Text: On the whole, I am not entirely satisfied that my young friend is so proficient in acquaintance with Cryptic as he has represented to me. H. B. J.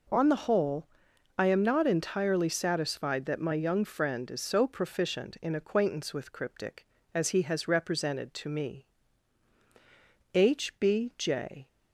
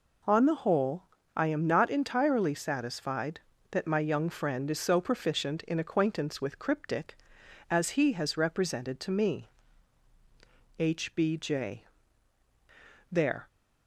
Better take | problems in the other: first | goes on to say "There"; slight; from 13.1 s on; 0.36 s long

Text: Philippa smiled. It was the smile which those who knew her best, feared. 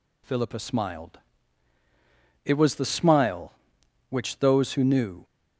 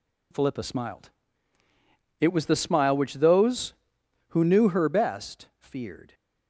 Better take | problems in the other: second | stops before "her best feared"; at 5.2 s

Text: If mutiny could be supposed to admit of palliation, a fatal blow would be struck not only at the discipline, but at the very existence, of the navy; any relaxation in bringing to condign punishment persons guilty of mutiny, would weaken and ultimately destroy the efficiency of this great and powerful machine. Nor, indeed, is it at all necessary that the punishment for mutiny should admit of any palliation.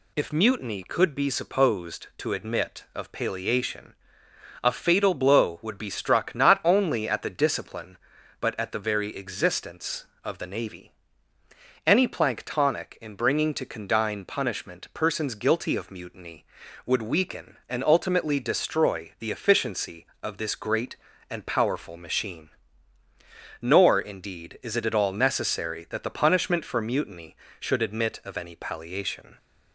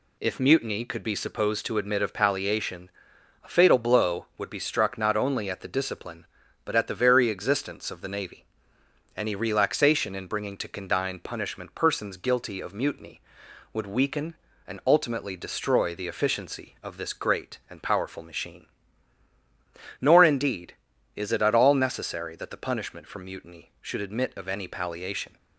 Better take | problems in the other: second | says "planktonic" for "relaxation"; at 12.0 s

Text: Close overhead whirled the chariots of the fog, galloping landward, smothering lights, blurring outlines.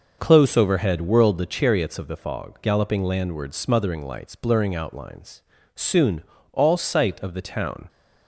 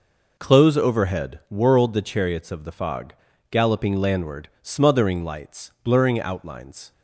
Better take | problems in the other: second | goes on to say "Soon all sight of the town"; strong; from 5.7 s on; 2.1 s long

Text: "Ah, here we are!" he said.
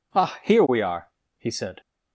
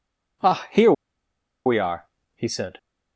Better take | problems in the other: first | pauses between "here" and "we"; noticeable; at 0.9 s; 0.73 s long

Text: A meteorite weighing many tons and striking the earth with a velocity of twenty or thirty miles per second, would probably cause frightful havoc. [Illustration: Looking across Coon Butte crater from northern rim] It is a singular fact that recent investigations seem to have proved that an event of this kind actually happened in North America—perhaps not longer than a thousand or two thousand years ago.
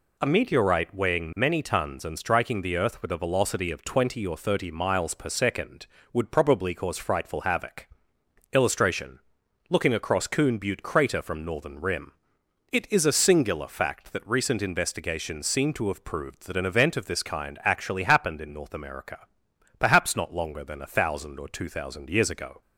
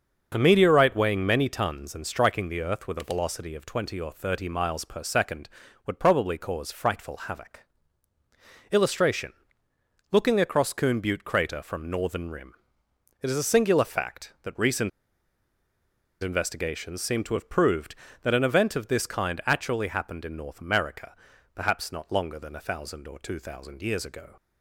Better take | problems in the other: first | starts louder than the rest; until 1.3 s; 6 dB // pauses between "rim" and "It"; noticeable; at 12.5 s; 0.66 s long; noticeable in the first // pauses between "recent" and "investigations"; strong; at 14.8 s; 1.3 s long

